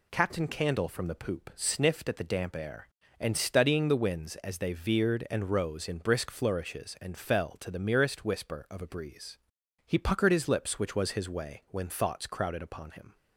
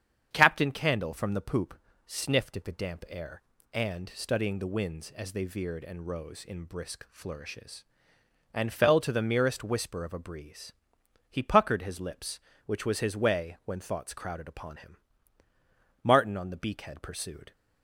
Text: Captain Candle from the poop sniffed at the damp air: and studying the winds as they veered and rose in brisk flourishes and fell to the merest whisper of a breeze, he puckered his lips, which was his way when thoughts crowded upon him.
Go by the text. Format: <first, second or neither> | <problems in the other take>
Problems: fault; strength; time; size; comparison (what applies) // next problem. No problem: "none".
first | starts louder than the rest; strong; until 1.3 s; 8 dB // pauses between "poop" and "sniffed"; slight; at 1.7 s; 0.28 s long // goes on to say "Martin on the beakhead pursued"; from 16.0 s on; 1.5 s long